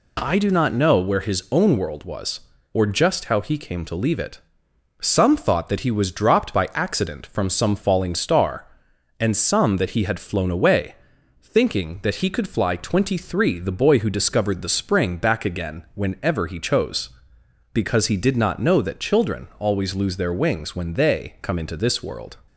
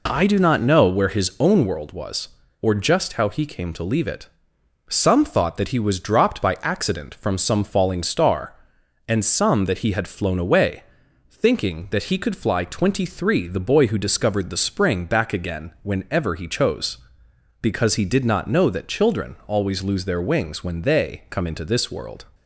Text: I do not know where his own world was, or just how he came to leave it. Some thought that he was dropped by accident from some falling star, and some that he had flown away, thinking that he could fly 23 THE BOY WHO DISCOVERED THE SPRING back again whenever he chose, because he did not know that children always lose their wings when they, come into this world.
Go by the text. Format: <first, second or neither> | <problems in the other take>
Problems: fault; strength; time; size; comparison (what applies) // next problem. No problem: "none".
first | starts louder than the rest; until 1.7 s; 3.5 dB